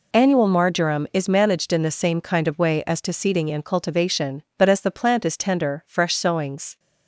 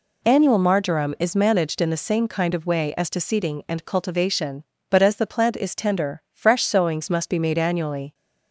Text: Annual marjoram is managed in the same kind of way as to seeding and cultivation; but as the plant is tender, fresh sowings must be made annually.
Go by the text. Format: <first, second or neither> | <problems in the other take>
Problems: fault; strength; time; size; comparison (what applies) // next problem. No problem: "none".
second | stops before "must be made annually"; at 6.7 s